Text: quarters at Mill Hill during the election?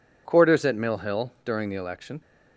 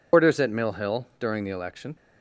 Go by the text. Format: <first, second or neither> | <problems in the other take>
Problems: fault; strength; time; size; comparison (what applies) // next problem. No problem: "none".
first | loses the start of "quarters"; at 0.1 s; 120 ms